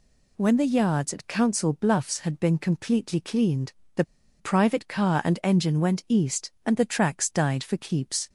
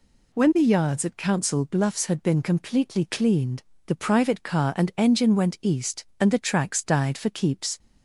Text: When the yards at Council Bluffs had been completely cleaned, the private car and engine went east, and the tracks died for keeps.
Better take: second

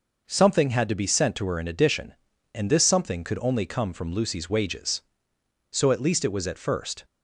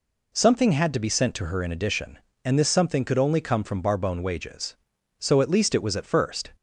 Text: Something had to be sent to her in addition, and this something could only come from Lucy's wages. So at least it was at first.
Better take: first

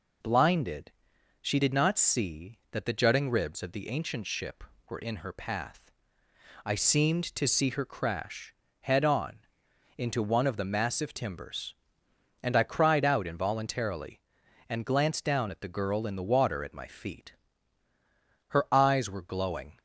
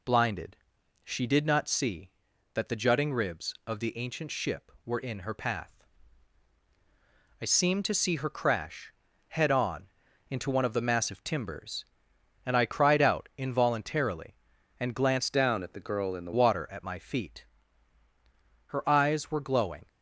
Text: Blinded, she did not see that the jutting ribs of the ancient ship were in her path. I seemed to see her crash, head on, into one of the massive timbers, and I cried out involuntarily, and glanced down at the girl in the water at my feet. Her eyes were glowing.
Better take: first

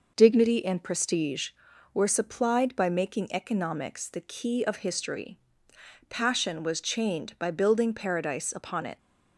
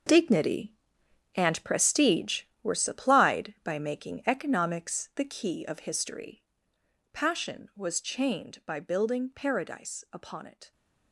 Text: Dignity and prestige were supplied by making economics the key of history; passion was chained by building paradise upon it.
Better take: first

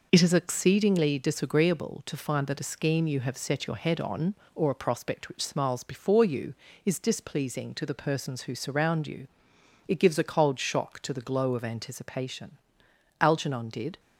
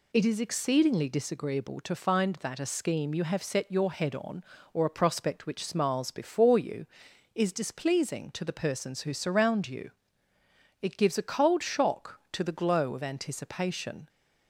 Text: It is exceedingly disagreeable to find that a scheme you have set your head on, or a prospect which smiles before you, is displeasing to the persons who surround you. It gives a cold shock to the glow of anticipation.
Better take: second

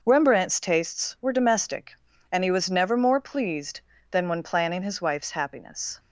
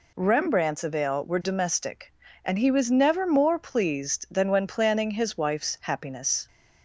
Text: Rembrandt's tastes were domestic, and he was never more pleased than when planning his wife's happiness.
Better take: first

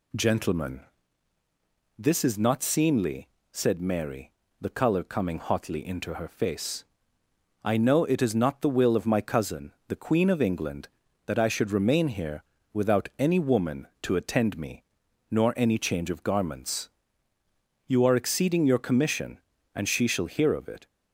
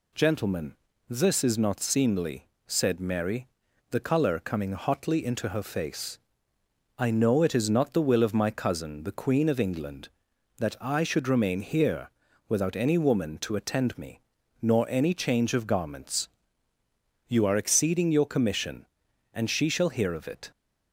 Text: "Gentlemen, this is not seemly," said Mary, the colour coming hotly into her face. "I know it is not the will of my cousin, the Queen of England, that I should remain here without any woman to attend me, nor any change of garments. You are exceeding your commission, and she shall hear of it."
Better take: neither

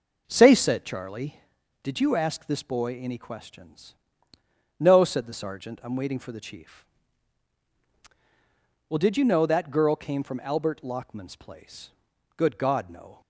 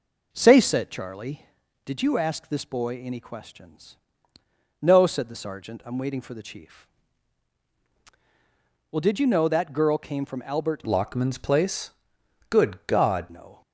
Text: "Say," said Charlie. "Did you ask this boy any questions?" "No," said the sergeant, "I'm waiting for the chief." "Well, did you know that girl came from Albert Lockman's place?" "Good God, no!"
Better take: first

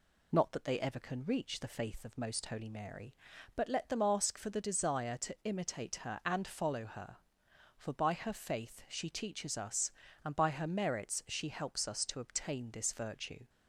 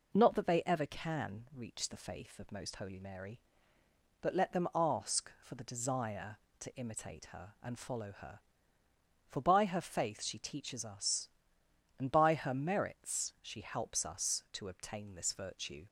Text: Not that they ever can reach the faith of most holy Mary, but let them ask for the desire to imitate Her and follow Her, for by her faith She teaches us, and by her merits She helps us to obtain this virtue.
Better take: neither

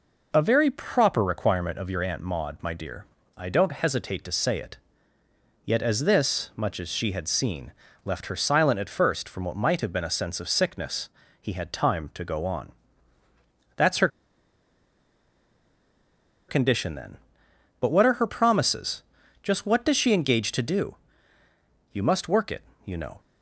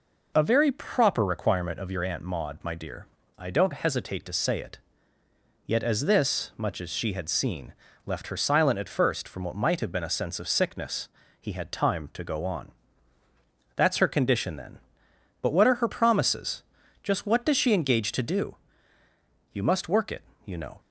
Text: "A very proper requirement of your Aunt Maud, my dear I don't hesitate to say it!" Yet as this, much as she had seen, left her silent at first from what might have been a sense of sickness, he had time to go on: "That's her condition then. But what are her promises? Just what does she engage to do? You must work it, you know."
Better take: second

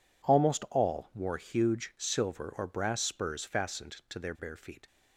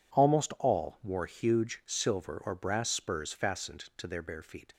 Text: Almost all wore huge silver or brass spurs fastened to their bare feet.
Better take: neither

